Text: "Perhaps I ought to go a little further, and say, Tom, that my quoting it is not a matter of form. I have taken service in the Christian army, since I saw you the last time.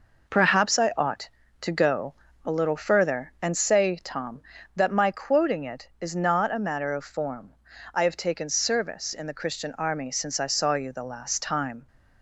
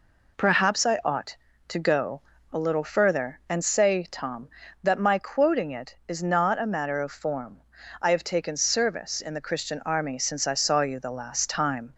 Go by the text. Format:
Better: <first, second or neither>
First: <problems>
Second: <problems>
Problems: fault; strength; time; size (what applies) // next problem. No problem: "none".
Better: second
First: gets quieter; throughout; 7 dB // pauses between "go" and "a"; slight; at 2.1 s; 0.32 s long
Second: pauses between "go" and "a"; slight; at 2.2 s; 0.32 s long